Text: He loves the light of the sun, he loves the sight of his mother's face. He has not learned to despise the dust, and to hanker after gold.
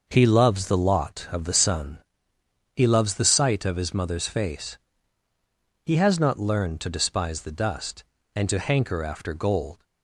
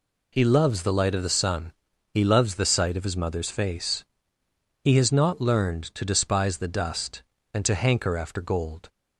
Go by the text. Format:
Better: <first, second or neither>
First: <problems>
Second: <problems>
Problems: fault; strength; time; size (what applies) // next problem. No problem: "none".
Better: second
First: says "lot" for "light"; at 0.7 s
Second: none